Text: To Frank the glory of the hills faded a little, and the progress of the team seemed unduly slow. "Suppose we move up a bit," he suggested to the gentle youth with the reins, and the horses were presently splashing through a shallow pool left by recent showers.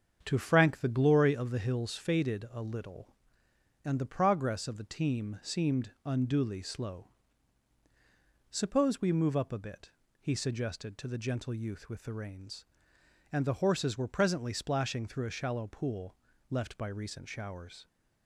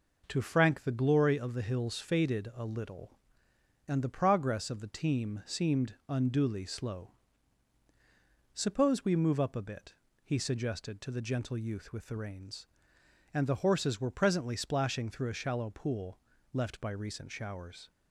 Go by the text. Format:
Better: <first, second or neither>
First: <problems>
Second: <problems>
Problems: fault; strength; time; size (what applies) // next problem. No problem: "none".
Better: second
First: starts louder than the rest; strong; until 1.8 s; 7.5 dB // pauses between "pool" and "left"; slight; at 16.1 s; 0.34 s long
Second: pauses between "pool" and "left"; slight; at 16.1 s; 0.34 s long